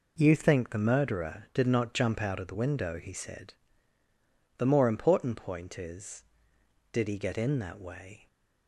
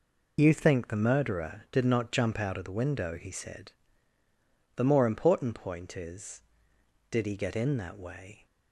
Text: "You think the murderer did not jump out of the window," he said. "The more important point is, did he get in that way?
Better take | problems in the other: first | loses the start of "You"; at 0.3 s; 35 ms

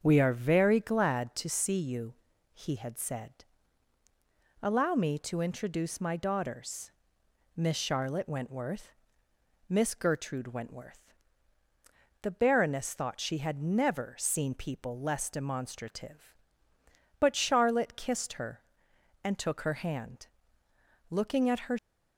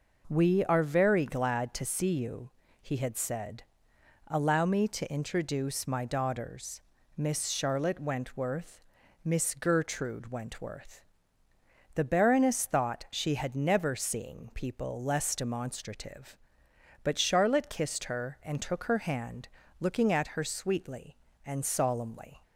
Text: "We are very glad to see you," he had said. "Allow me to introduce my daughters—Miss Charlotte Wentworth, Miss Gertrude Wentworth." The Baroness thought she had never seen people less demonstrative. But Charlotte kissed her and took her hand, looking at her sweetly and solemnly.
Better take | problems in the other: second | starts louder than the rest; until 1.0 s; 7 dB // stops before "sweetly and solemnly"; at 21.7 s

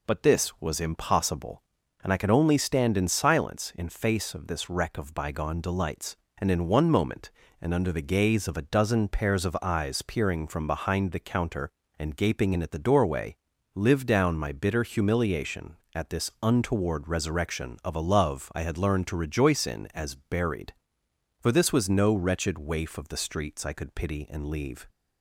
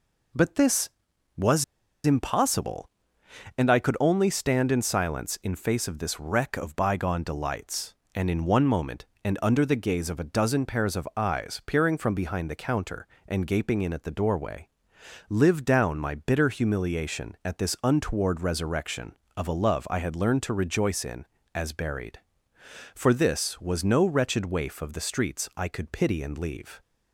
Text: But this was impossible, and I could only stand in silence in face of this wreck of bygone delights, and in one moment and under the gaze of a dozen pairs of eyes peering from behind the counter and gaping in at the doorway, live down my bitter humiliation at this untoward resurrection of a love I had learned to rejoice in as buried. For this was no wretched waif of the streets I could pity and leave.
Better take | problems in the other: first | pauses between "was" and "impossible"; at 1.6 s; 0.40 s long

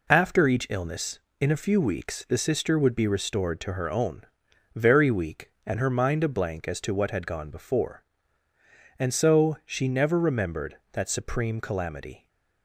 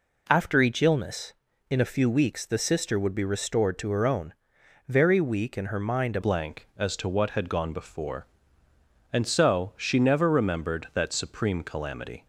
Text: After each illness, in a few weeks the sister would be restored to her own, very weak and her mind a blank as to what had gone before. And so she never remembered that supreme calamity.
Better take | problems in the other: first | changes voice at "blank"; from 6.2 s on; 6.0 s long

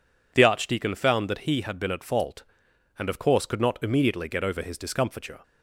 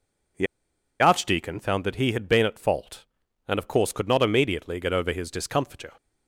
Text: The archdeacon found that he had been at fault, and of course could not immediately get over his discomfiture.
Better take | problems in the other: first | pauses between "The" and "archdeacon"; noticeable; at 0.4 s; 0.55 s long

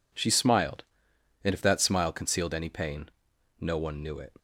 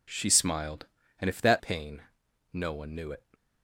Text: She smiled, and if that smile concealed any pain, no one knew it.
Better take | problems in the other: first | skips "smile concealed any"; at 1.5 s

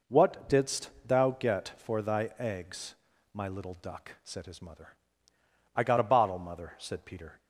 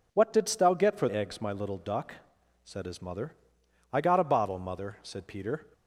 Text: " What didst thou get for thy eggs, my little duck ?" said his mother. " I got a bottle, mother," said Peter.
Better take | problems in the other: first | skips "thy"; at 1.0 s

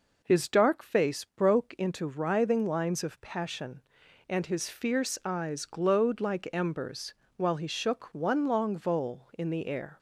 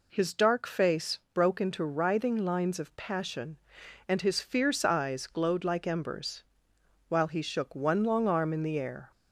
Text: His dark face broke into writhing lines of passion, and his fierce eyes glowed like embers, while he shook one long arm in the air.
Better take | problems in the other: second | says "vole" for "arm"; at 8.7 s

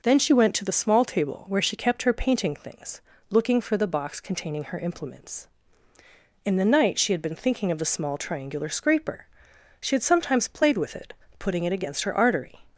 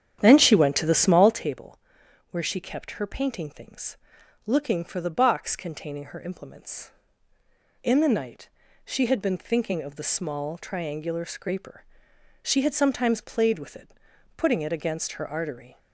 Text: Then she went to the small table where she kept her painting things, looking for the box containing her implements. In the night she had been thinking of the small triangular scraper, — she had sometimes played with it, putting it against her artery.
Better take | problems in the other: first | starts louder than the rest; strong; until 1.5 s; 9 dB // pauses between "table" and "where"; noticeable; at 1.7 s; 0.52 s long // pauses between "night" and "she"; slight; at 8.4 s; 0.36 s long

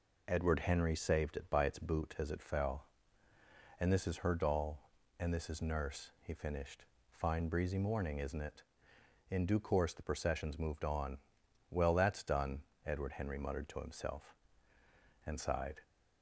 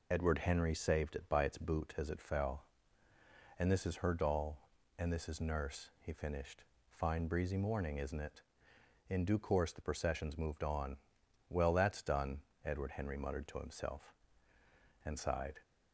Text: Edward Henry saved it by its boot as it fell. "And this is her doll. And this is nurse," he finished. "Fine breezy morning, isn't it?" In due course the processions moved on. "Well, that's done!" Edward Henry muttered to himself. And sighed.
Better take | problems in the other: first | loses the start of "Edward"; at 0.1 s; 40 ms

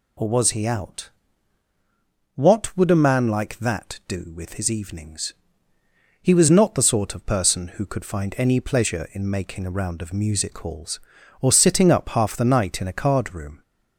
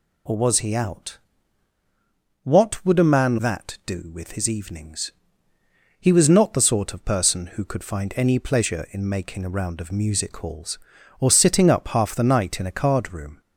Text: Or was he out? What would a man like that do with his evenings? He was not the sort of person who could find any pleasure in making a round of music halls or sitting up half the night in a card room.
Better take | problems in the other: first | skips "like"; at 3.3 s

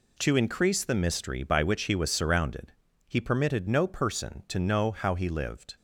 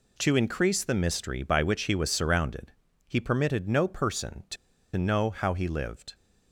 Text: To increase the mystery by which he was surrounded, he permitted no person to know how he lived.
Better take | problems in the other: first | pauses between "to" and "know"; at 4.5 s; 0.40 s long

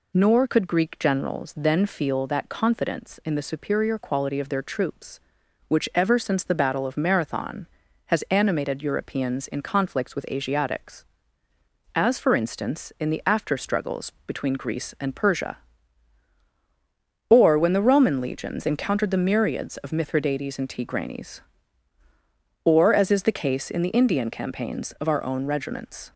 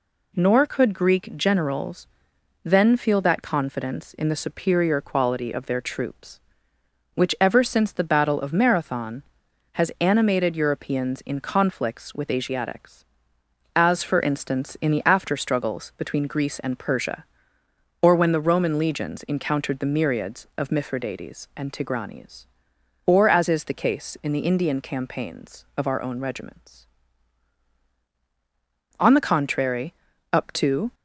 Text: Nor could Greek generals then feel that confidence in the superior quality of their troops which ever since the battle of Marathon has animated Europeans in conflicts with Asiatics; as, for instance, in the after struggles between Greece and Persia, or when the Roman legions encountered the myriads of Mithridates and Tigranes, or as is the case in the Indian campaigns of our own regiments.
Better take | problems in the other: first | pauses between "generals" and "then"; noticeable; at 2.0 s; 0.56 s long // goes on to say "On the contrary up to"; strong; from 28.9 s on; 1.9 s long

